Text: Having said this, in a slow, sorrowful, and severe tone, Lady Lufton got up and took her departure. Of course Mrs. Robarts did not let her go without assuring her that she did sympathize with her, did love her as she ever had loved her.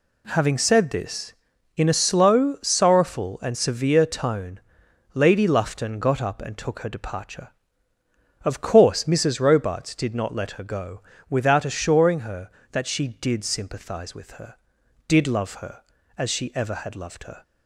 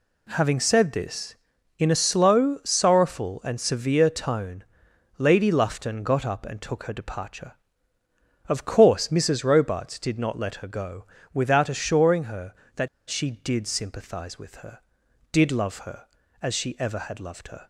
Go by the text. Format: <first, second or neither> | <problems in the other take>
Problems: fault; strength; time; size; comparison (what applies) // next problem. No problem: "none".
first | pauses between "go" and "without"; slight; at 11.0 s; 0.26 s long; slight in the first // pauses between "that" and "she"; slight; at 12.8 s; 0.20 s long